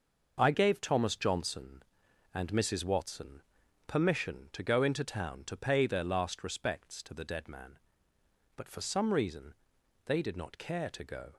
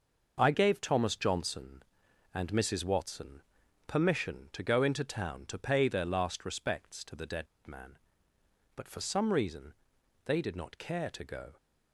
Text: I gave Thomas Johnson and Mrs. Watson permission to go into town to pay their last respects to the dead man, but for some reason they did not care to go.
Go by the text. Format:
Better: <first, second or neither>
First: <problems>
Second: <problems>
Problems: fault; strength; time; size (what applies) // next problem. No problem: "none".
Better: first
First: pauses between "Watson" and "permission"; noticeable; at 3.4 s; 0.46 s long // pauses between "reason" and "they"; noticeable; at 9.5 s; 0.50 s long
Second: pauses between "Watson" and "permission"; noticeable; at 3.4 s; 0.46 s long // pauses between "dead" and "man"; slight; at 7.4 s; 0.19 s long // pauses between "reason" and "they"; noticeable; at 9.7 s; 0.50 s long